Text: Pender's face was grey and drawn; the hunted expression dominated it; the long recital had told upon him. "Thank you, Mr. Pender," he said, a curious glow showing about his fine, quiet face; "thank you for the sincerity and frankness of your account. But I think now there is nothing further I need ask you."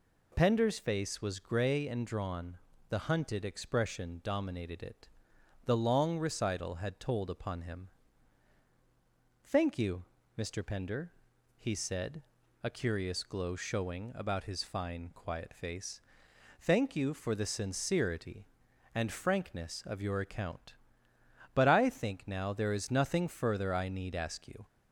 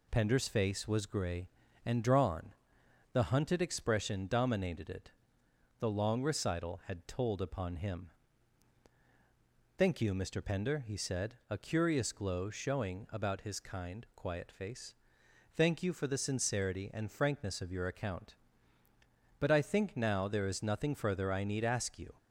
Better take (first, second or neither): first